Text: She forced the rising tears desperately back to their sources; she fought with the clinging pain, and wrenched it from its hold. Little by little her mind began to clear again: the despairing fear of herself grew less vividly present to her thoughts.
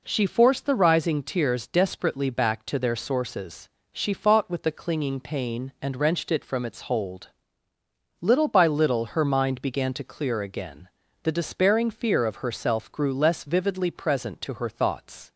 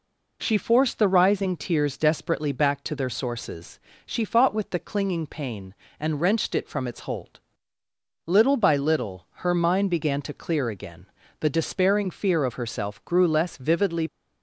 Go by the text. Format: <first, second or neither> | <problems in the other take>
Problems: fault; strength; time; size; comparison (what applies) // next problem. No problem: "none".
first | pauses between "little" and "her"; slight; at 9.2 s; 0.18 s long // stops before "present to her thoughts"; at 14.0 s